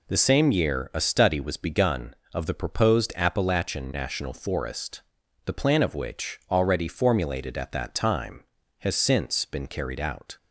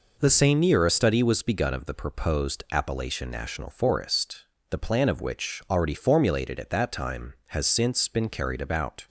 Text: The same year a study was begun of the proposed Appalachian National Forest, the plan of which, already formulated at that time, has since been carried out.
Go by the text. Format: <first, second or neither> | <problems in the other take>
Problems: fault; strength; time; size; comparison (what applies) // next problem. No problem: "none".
first | says "about" for "out"; at 8.6 s